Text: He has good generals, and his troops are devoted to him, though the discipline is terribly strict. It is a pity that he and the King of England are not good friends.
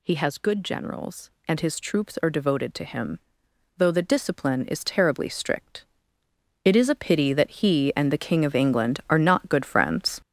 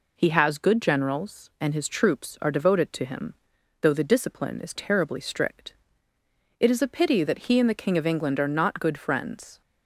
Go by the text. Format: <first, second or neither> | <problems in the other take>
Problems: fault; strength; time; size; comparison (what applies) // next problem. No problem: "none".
second | gets louder; throughout; 7 dB